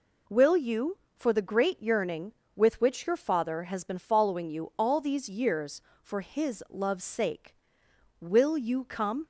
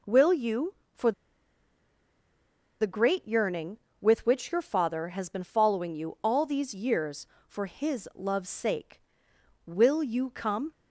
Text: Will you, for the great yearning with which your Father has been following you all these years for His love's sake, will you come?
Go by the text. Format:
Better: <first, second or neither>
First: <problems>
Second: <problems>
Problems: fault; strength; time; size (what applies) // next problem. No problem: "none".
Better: first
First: none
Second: pauses between "for" and "the"; strong; at 1.1 s; 1.6 s long